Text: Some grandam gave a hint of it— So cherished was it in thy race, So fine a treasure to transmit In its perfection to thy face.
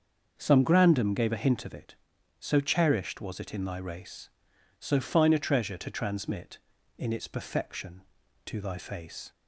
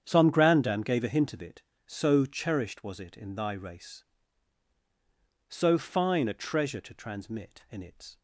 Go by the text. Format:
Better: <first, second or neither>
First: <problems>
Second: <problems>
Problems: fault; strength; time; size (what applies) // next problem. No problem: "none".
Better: first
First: starts louder than the rest; until 1.3 s; 6.5 dB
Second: starts louder than the rest; strong; until 1.0 s; 8.5 dB // stops before "perfection to thy face"; at 8.1 s